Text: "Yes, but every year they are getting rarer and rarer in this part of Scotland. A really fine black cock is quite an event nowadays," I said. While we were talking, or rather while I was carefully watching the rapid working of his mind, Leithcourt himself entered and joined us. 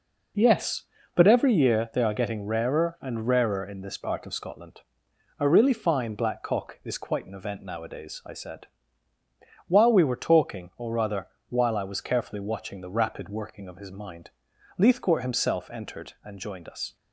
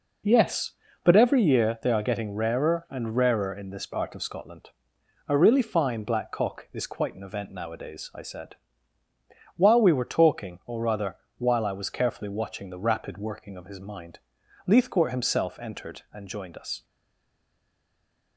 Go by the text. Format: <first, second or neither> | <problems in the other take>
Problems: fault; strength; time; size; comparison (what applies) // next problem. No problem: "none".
first | pauses between "rather" and "while"; slight; at 11.1 s; 0.20 s long; slight in the first // stays silent after the last word; noticeable; from 16.8 s on; 1.5 s long